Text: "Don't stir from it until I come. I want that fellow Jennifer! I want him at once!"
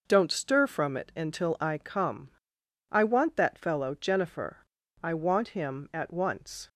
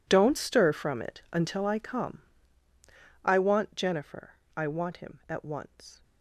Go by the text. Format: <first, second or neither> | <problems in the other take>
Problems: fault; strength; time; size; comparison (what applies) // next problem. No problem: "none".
first | skips "that fellow"; at 3.7 s